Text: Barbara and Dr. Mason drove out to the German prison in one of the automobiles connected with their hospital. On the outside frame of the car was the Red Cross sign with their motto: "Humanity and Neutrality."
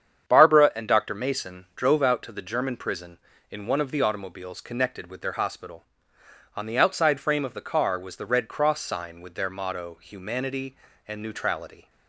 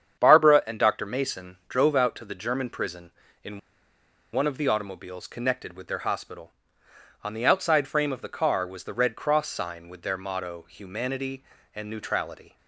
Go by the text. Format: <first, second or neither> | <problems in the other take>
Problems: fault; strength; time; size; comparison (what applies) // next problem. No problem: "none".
first | starts louder than the rest; strong; until 1.2 s; 8 dB; strong in the first // pauses between "in" and "one"; noticeable; at 3.5 s; 0.73 s long